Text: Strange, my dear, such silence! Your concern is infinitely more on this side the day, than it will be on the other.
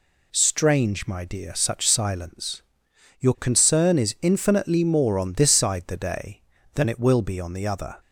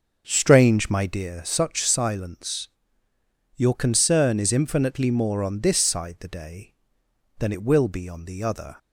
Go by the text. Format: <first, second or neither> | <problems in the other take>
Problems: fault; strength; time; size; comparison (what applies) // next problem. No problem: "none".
first | starts louder than the rest; until 1.2 s; 6.5 dB